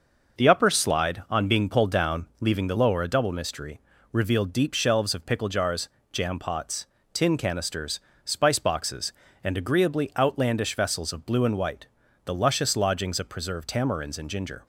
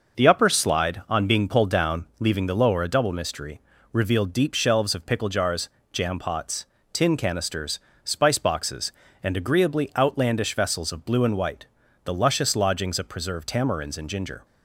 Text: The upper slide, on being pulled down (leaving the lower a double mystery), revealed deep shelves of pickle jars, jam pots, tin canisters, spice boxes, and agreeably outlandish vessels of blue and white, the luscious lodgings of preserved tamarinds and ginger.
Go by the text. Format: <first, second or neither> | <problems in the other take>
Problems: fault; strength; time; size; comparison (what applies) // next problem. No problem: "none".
neither | none